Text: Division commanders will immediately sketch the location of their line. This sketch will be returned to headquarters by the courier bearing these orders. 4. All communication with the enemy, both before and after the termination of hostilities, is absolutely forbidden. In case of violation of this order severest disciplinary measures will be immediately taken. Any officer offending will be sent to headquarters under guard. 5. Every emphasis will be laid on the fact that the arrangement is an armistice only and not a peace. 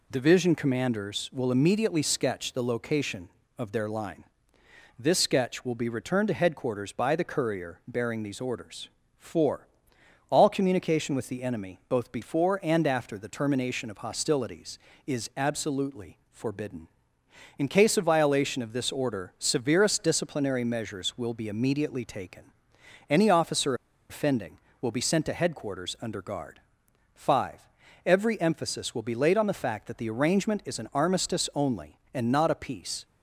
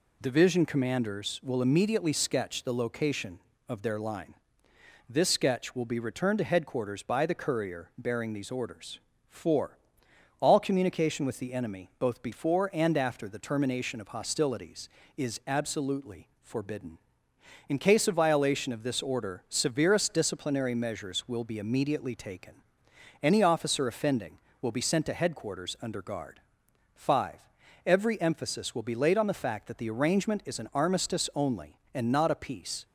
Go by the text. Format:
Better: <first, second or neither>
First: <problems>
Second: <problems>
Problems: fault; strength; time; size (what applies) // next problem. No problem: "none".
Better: second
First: pauses between "officer" and "offending"; slight; at 23.7 s; 0.35 s long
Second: none